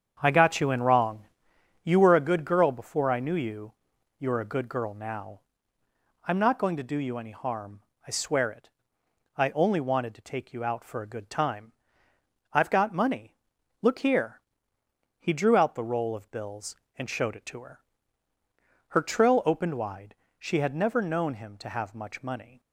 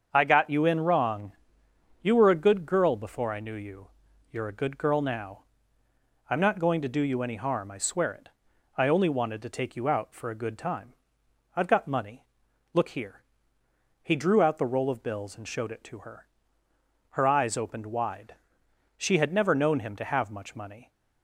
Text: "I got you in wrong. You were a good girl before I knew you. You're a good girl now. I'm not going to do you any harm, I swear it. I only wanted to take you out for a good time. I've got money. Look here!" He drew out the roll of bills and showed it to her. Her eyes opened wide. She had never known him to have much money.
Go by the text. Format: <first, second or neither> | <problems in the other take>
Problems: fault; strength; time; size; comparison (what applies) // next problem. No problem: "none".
second | starts louder than the rest; strong; until 1.2 s; 7.5 dB; also in the second // says "trill" for "eyes"; at 19.0 s